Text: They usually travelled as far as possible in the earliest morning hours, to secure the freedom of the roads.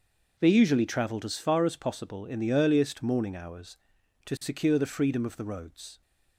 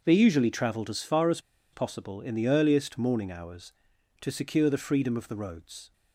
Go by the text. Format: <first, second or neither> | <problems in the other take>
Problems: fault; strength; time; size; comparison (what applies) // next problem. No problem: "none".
first | starts louder than the rest; noticeable; until 1.0 s; 6 dB; noticeable in the first // pauses between "as" and "possible"; slight; at 1.3 s; 0.32 s long